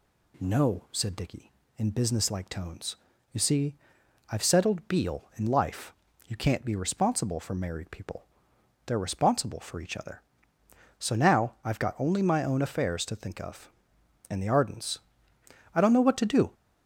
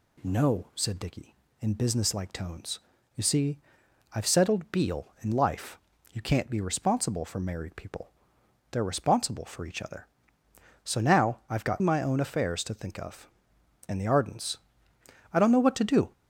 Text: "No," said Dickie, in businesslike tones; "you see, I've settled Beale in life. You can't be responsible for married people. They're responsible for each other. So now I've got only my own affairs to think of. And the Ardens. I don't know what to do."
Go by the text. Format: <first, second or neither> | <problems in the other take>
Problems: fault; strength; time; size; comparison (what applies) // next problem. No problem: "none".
first | skips "only"; at 11.8 s